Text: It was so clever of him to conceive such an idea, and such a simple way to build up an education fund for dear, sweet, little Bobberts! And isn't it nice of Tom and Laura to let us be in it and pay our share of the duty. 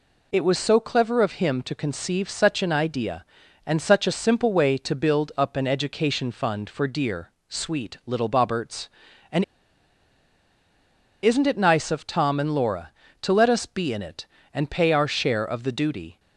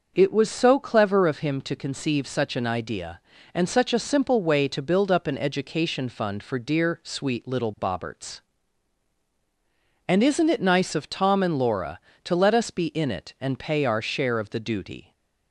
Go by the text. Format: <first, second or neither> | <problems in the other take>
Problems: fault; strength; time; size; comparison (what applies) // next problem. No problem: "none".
second | pauses between "And" and "isn't"; strong; at 9.4 s; 1.7 s long